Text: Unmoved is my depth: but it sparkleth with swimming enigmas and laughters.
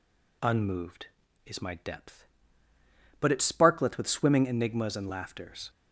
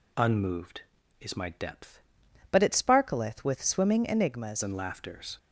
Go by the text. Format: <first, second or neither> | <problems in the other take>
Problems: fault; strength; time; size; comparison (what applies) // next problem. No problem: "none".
first | changes voice from "but" to "enigmas"; from 2.5 to 4.6 s; 2.1 s long